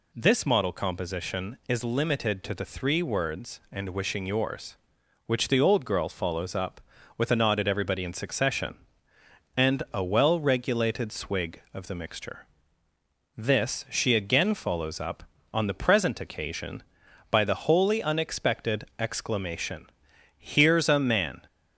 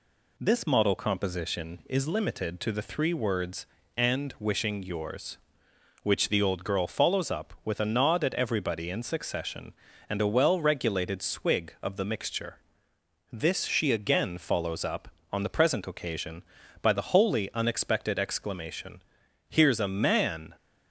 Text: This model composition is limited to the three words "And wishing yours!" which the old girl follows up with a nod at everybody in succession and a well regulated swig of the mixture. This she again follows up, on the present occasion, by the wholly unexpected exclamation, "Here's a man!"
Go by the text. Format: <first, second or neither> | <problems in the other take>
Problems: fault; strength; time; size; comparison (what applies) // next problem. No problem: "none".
neither | none